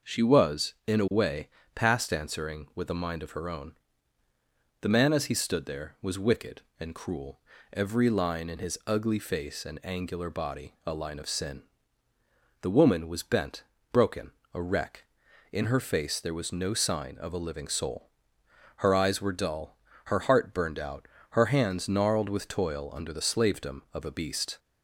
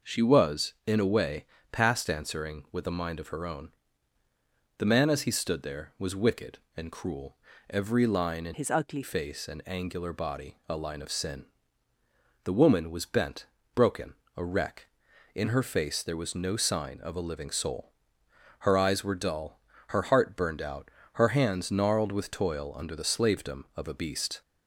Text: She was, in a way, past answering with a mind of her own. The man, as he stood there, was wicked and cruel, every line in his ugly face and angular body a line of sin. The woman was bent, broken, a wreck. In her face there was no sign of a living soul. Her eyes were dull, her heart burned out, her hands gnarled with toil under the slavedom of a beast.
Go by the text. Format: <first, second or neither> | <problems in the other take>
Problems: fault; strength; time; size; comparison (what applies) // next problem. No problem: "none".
first | changes voice from "his" to "ugly"; from 8.5 to 9.0 s; 0.5 s long